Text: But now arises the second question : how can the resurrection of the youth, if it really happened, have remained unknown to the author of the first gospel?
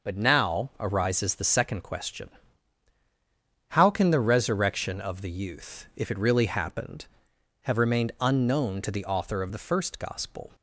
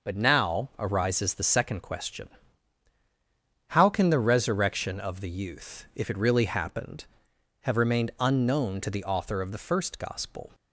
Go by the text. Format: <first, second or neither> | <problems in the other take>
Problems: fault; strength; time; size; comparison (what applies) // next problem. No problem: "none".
neither | none